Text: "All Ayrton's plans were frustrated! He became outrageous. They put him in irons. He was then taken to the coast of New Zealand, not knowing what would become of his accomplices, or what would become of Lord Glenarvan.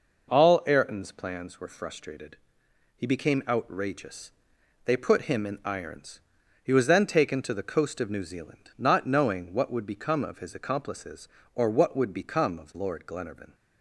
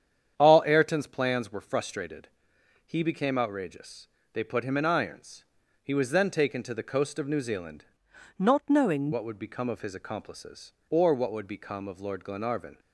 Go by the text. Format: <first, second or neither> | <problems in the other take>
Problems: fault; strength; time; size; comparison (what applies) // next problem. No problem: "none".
first | starts louder than the rest; strong; until 1.3 s; 8.5 dB // changes voice from "not" to "knowing"; from 8.3 to 9.1 s; 0.8 s long